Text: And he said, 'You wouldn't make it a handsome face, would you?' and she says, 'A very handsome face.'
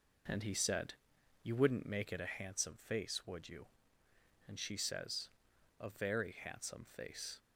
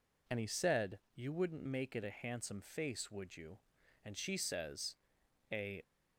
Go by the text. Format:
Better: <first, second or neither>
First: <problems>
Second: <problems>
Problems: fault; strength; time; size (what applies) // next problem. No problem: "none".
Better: first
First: none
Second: stops before "very handsome face"; at 5.8 s